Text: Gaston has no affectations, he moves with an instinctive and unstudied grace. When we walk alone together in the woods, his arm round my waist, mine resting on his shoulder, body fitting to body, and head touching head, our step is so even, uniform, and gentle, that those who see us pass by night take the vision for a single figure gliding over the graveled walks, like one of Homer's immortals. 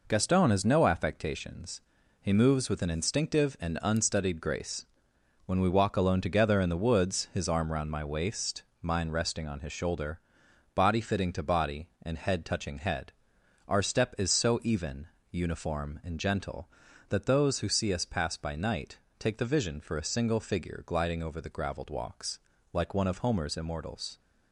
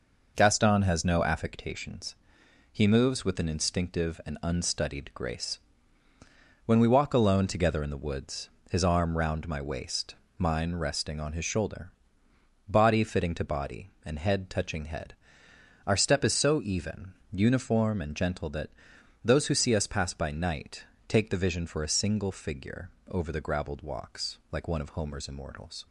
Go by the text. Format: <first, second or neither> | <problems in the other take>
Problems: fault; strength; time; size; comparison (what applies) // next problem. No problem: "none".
first | pauses between "that" and "those"; noticeable; at 18.6 s; 0.56 s long // pauses between "night" and "take"; slight; at 20.8 s; 0.24 s long; slight in the first // skips "gliding"; at 22.9 s